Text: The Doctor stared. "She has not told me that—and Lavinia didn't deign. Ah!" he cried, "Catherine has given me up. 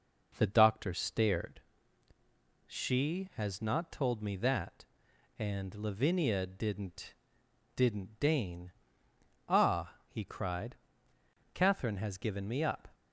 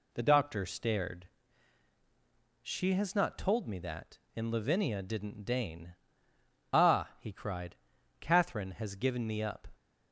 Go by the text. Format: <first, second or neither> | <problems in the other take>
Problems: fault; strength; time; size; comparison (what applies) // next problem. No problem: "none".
second | says "didn't" twice; at 7.7 s